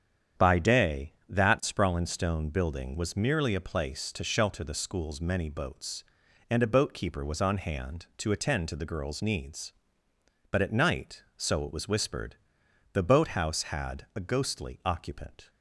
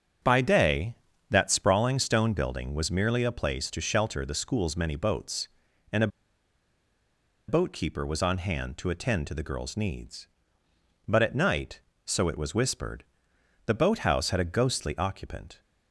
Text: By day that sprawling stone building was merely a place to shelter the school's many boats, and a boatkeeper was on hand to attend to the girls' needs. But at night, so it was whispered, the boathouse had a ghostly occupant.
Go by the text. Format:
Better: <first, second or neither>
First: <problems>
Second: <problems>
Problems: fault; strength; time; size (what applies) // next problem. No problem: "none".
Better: first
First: starts louder than the rest; strong; until 1.5 s; 8.5 dB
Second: starts louder than the rest; strong; until 1.6 s; 7.5 dB // pauses between "a" and "boatkeeper"; strong; at 6.0 s; 1.4 s long